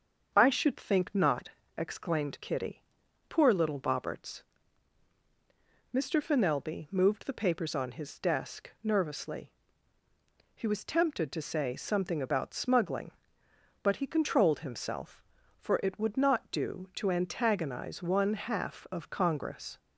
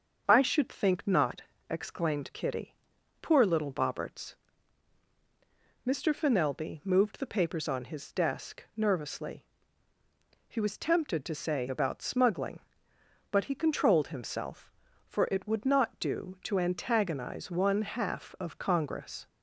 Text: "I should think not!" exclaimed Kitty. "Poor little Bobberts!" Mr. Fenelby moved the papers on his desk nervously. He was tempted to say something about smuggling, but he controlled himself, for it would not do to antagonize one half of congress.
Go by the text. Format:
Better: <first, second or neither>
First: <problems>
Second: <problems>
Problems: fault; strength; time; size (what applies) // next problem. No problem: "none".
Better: first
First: starts louder than the rest; until 1.3 s; 7 dB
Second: starts louder than the rest; until 1.2 s; 7 dB // skips "something"; at 11.6 s